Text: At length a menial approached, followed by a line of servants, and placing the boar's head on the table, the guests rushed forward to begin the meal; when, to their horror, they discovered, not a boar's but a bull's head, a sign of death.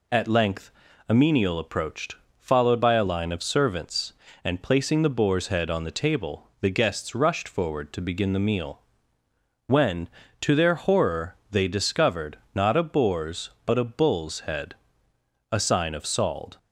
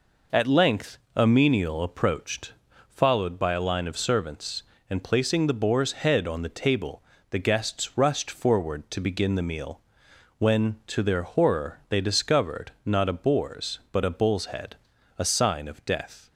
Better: second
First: pauses between "length" and "a"; at 0.7 s; 0.38 s long // says "sald" for "death"; at 16.0 s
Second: pauses between "length" and "a"; slight; at 0.9 s; 0.16 s long

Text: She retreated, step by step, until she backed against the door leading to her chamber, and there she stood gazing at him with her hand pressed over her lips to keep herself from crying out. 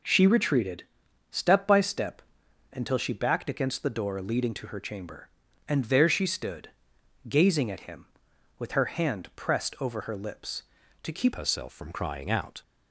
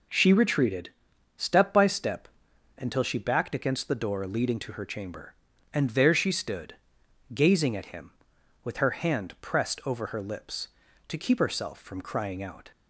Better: second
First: pauses between "stood" and "gazing"; noticeable; at 6.6 s; 0.60 s long // changes voice at "herself"; from 11.3 s on; 1.3 s long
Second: pauses between "stood" and "gazing"; noticeable; at 6.7 s; 0.60 s long

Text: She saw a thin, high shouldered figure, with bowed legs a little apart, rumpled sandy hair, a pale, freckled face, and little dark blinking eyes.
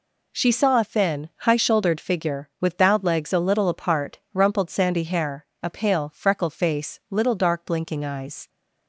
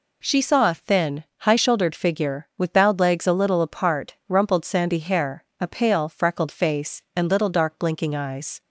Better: second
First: skips "and"; at 7.0 s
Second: none

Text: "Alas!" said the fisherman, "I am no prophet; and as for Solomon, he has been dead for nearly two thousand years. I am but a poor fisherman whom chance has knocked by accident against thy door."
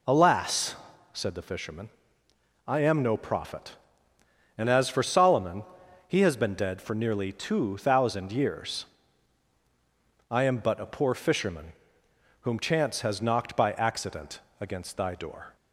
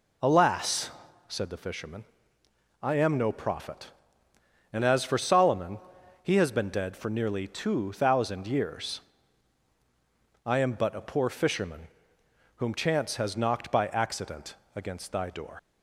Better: first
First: pauses between "fisherman" and "whom"; noticeable; at 11.7 s; 0.68 s long // pauses between "accident" and "against"; slight; at 14.4 s; 0.20 s long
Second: pauses between "fisherman" and "whom"; noticeable; at 11.8 s; 0.68 s long // pauses between "accident" and "against"; slight; at 14.5 s; 0.20 s long // leaves "door" unfinished; at 15.5 s; 105 ms

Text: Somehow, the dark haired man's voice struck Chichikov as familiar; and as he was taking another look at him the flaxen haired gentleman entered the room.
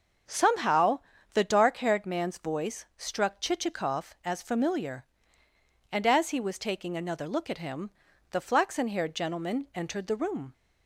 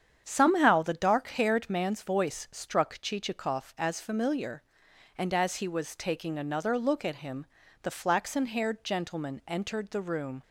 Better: neither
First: starts louder than the rest; strong; until 1.6 s; 7.5 dB // pauses between "him" and "the"; at 7.9 s; 0.40 s long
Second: starts louder than the rest; strong; until 1.2 s; 8 dB // pauses between "him" and "the"; at 7.4 s; 0.38 s long

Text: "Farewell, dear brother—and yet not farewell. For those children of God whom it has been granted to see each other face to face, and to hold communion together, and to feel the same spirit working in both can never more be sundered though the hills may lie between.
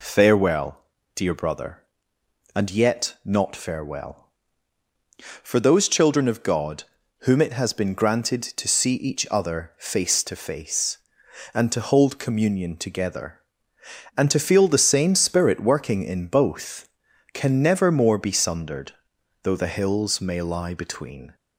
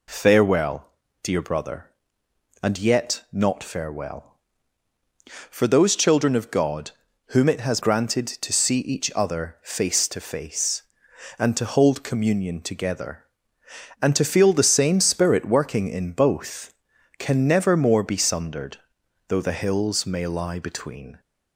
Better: first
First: pauses between "God" and "whom"; at 6.8 s; 0.38 s long // pauses between "sundered" and "though"; noticeable; at 18.9 s; 0.50 s long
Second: pauses between "God" and "whom"; at 6.8 s; 0.38 s long // skips "been"; at 7.7 s // pauses between "sundered" and "though"; noticeable; at 18.7 s; 0.50 s long

